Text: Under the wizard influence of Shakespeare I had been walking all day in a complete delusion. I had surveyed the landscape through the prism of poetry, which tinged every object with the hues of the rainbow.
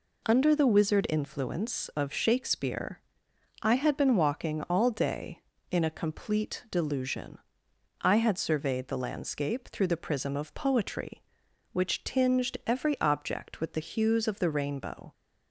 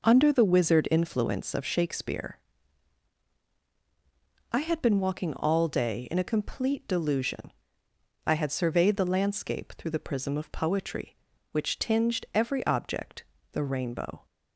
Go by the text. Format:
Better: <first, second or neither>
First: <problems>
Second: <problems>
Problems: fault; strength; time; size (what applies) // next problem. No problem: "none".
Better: first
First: pauses between "Shakespeare" and "I"; noticeable; at 3.0 s; 0.60 s long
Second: pauses between "Shakespeare" and "I"; strong; at 2.3 s; 2.1 s long // skips "with the hues of"; at 13.3 s